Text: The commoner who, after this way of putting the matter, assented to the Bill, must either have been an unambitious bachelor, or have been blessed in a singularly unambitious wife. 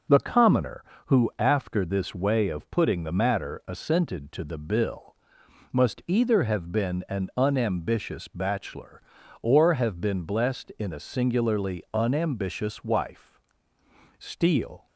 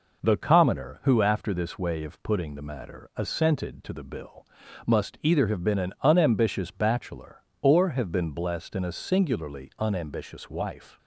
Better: second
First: goes on to say "Steele"; noticeable; from 14.1 s on; 0.68 s long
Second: none

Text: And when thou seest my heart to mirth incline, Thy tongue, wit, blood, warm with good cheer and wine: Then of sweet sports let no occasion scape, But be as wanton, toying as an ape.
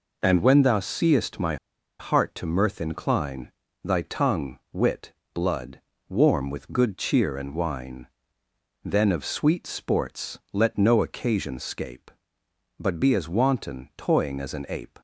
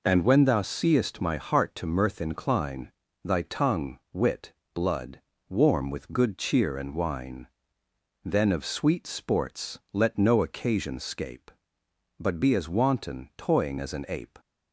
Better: second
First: pauses between "my" and "heart"; at 1.5 s; 0.43 s long // pauses between "sports" and "let"; slight; at 10.3 s; 0.16 s long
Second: pauses between "sports" and "let"; slight; at 9.7 s; 0.16 s long

